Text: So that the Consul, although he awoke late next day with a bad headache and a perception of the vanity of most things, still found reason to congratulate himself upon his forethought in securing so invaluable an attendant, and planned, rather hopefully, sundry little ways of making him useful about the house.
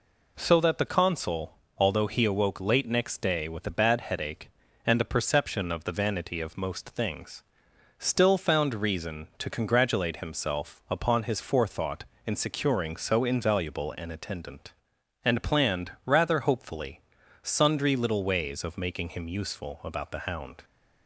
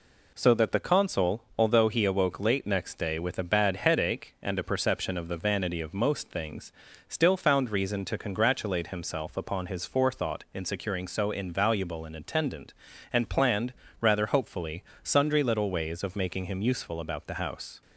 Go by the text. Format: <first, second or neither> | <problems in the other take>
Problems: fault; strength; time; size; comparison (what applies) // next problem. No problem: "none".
second | says "hound" for "house"; at 20.1 s